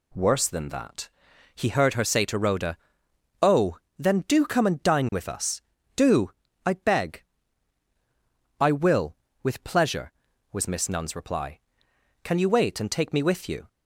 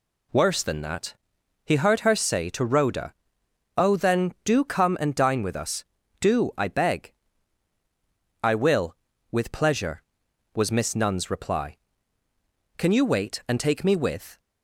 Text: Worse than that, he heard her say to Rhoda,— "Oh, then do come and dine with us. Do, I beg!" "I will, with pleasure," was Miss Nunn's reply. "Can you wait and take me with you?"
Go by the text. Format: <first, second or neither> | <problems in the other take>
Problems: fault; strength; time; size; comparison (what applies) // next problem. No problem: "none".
first | stops before "you"; at 14.3 s